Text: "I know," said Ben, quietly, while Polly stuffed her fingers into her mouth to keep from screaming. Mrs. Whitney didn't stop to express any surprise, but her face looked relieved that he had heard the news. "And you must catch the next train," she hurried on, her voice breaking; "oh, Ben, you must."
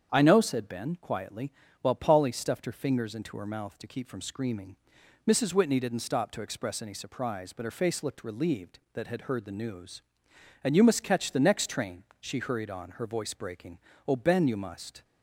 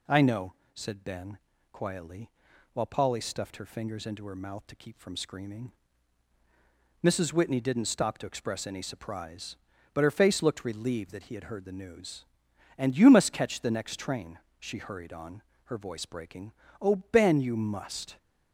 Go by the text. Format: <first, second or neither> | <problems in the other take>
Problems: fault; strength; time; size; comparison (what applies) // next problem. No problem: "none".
second | starts louder than the rest; strong; until 1.1 s; 8 dB // skips "he"; at 9.0 s